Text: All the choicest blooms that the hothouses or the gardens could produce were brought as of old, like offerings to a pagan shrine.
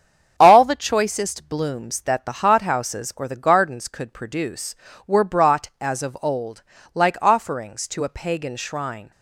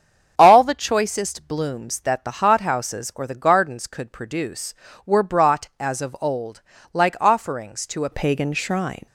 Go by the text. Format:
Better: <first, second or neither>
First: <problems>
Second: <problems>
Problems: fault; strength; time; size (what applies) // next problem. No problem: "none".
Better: first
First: starts louder than the rest; strong; until 1.3 s; 8 dB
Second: starts louder than the rest; strong; until 1.3 s; 7.5 dB // changes voice at "pagan"; from 8.1 s on; 0.9 s long